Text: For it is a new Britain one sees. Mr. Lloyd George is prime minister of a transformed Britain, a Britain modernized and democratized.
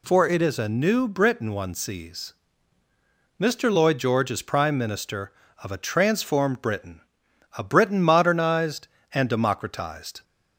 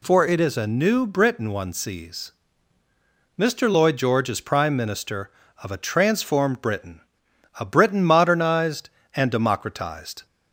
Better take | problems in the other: neither | none

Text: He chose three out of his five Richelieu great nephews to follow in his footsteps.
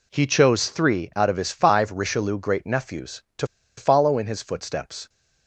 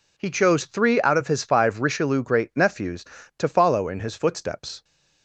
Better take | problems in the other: second | pauses between "to" and "follow"; slight; at 3.4 s; 0.32 s long

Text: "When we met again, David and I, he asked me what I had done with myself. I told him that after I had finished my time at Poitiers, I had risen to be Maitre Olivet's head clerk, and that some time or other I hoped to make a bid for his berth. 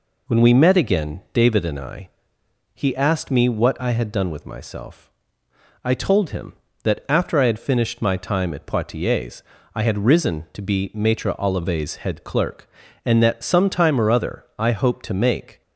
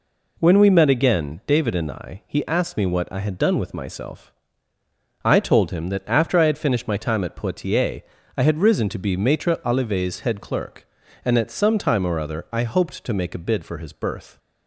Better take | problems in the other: second | stops before "a bid for his berth"; at 15.6 s

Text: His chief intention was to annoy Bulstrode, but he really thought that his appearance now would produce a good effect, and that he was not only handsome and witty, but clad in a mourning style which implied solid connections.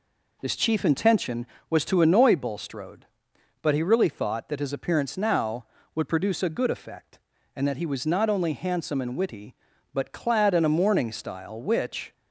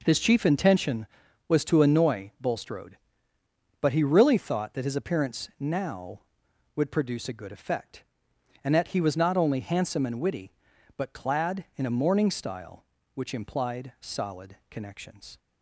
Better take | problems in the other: second | stops before "implied solid connections"; at 12.1 s

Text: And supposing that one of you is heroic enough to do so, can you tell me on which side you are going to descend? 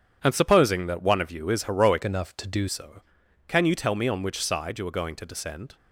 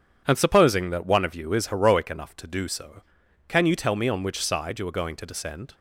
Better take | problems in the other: second | starts louder than the rest; strong; until 1.2 s; 8.5 dB // changes voice from "enough" to "do"; from 2.0 to 2.6 s; 0.6 s long

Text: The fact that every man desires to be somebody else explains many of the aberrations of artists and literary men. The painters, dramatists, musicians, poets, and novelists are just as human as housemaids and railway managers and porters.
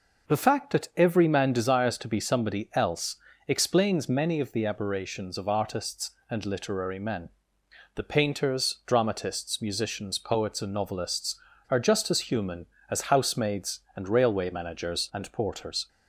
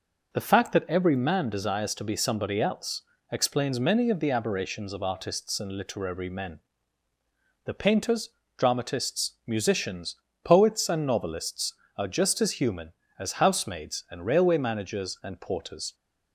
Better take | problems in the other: neither | pauses between "else" and "explains"; slight; the same in both

